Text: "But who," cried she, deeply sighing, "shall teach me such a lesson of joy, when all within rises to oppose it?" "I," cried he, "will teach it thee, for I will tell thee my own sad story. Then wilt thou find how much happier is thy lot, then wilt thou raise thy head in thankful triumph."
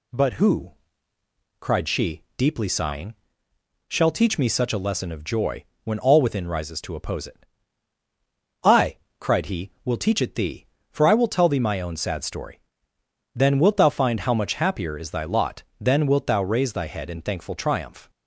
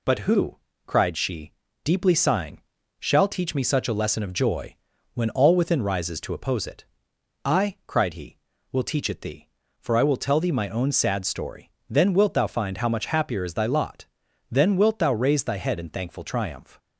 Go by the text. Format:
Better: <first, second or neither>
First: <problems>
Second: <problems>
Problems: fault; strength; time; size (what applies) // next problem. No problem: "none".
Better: neither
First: none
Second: none